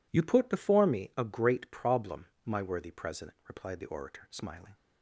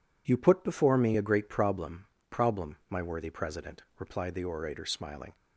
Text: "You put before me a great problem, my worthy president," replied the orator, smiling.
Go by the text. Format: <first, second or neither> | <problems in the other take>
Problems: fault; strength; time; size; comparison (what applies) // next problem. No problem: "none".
first | says "problem" twice; at 2.3 s